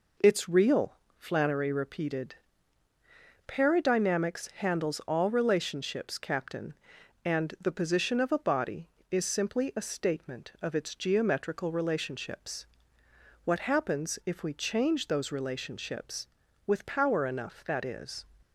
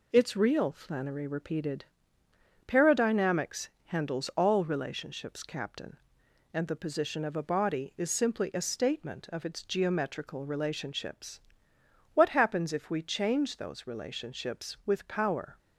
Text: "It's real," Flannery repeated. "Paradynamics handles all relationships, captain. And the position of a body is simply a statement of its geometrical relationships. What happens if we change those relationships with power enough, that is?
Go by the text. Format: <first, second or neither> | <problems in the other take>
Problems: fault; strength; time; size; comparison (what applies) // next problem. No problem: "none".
first | pauses between "Paradynamics" and "handles"; slight; at 3.6 s; 0.18 s long // stops before "enough that is"; at 15.5 s